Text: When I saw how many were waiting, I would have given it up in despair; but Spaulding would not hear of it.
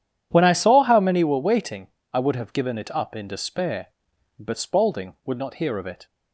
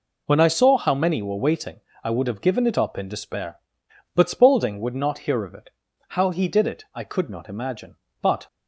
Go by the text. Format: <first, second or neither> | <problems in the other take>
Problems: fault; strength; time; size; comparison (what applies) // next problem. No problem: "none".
first | goes on to say "How he did it I could not imagine but"; strong; from 6.0 s on; 2.3 s long